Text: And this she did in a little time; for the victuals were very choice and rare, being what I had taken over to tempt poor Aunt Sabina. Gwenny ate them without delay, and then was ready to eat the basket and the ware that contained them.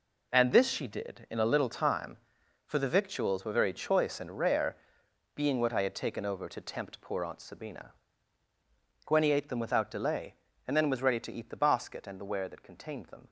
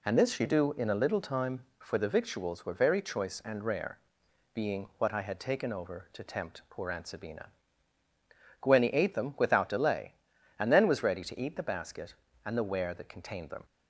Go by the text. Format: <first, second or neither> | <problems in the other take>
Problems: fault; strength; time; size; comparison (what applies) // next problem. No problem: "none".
first | says "do" for "did"; at 0.4 s